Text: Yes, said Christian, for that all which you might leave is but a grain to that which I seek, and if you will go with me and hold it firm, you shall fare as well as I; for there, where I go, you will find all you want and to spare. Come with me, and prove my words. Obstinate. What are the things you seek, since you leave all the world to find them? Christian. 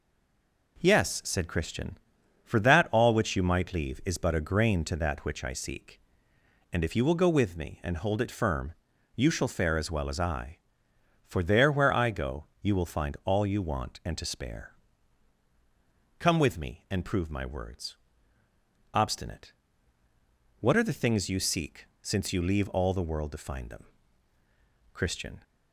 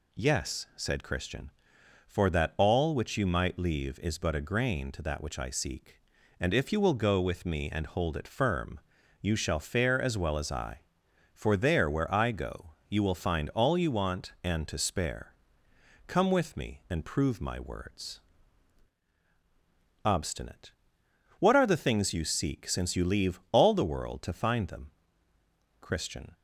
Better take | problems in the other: second | stays silent before the first word; slight; until 0.7 s; 0.7 s long

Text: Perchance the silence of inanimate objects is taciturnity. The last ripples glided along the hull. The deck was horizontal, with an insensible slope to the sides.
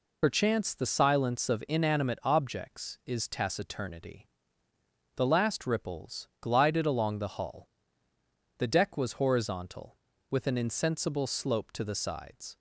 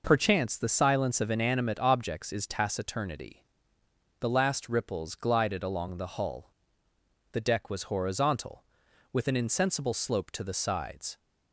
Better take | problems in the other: second | loses the start of "Perchance"; at 0.2 s; 45 ms

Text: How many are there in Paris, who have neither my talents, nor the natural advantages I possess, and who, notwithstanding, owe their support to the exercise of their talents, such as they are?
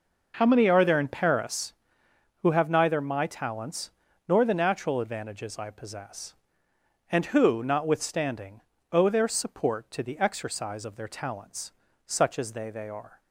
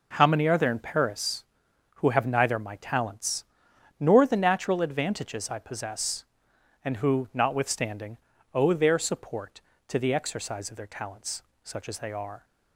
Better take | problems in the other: second | says "they" twice; at 12.7 s

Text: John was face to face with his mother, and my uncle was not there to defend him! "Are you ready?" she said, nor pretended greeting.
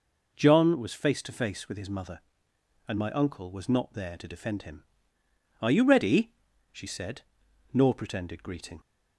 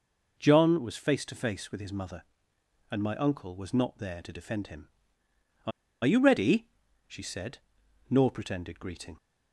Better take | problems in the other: first | pauses between "Are" and "you"; slight; at 5.7 s; 0.33 s long

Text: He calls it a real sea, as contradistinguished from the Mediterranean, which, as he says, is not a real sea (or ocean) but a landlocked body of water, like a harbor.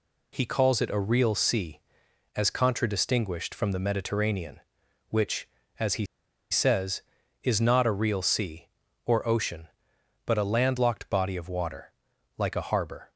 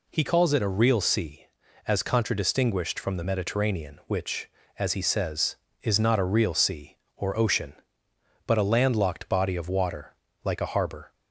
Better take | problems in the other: second | pauses between "he" and "says"; at 6.0 s; 0.45 s long

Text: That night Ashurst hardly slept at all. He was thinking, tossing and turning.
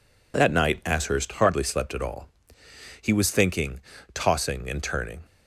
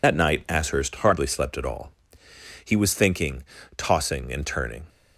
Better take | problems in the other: first | loses the start of "That"; at 0.0 s; 65 ms

